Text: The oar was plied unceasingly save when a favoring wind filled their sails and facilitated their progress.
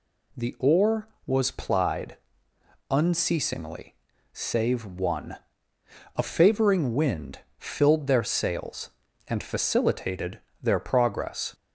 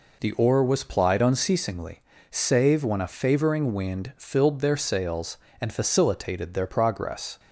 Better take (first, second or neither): second